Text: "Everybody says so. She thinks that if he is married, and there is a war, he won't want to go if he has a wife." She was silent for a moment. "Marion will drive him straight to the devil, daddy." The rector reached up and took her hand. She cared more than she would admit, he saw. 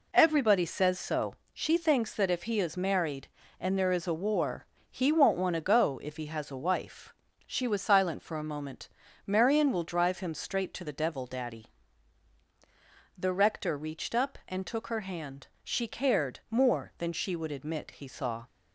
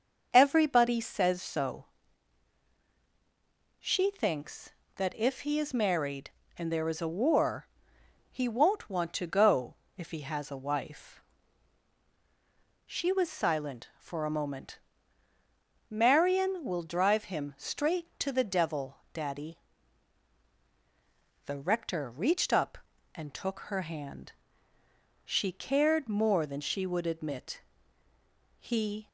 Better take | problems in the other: first | starts louder than the rest; until 1.3 s; 6.5 dB // pauses between "go" and "if"; slight; at 9.7 s; 0.22 s long // stops before "saw"; at 29.0 s

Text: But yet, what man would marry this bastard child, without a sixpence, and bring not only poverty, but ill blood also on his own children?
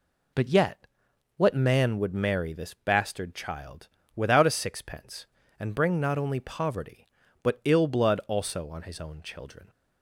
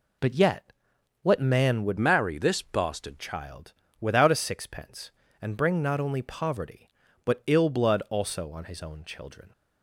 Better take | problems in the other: first | changes voice from "marry" to "bastard"; from 1.9 to 3.1 s; 1.2 s long

